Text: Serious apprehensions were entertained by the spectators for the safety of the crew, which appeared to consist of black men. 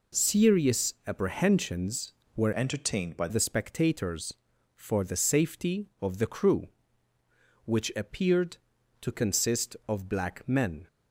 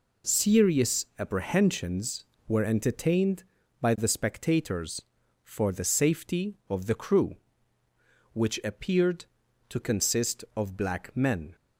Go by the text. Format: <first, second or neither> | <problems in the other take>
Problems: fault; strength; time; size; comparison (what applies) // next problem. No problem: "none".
second | changes voice from "entertained" to "by"; from 2.5 to 3.2 s; 0.7 s long